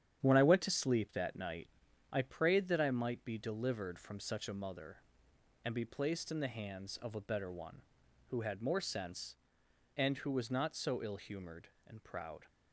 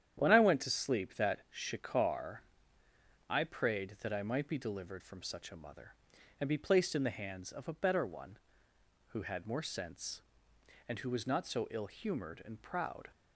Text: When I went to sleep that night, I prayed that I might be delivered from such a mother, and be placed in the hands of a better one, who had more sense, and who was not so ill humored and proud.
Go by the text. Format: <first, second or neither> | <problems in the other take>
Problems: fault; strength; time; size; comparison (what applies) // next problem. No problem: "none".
first | starts louder than the rest; strong; until 1.2 s; 9.5 dB; strong in the first // says "shikar" for "night"; at 1.4 s